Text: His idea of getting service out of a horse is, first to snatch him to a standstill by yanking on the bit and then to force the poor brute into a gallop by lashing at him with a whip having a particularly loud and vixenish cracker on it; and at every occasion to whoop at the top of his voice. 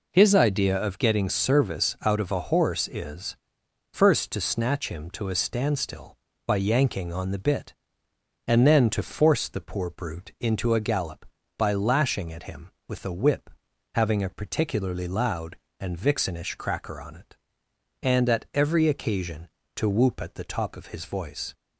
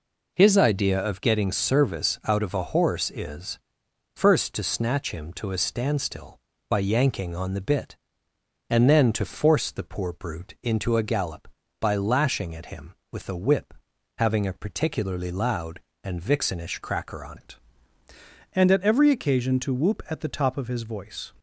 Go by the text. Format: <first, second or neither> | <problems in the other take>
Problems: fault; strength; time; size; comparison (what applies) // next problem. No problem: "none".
first | pauses between "whip" and "having"; at 13.7 s; 0.42 s long; also in the first // changes voice at "it"; from 17.3 s on; 4.0 s long